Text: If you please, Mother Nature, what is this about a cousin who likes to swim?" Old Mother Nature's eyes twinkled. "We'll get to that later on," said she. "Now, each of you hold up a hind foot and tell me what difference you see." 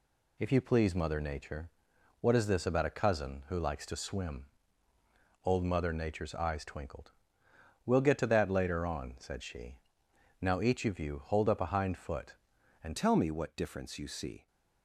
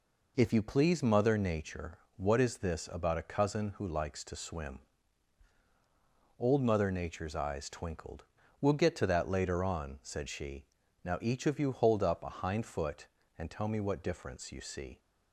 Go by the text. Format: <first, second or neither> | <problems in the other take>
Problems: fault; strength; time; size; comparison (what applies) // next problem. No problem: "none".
second | changes voice at "tell"; from 12.9 s on; 1.5 s long